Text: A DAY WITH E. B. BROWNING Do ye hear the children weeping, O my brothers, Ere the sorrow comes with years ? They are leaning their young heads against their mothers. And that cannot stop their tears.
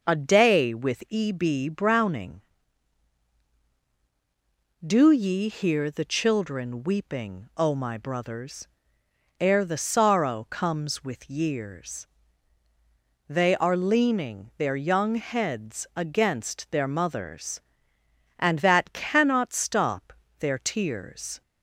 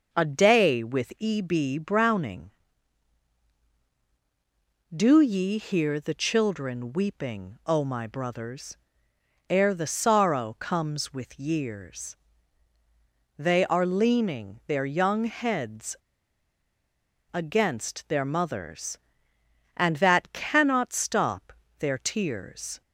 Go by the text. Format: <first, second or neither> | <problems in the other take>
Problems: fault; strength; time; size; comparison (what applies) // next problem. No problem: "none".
first | pauses between "heads" and "against"; strong; at 15.9 s; 1.3 s long // pauses between "stop" and "their"; slight; at 21.5 s; 0.26 s long; slight in the first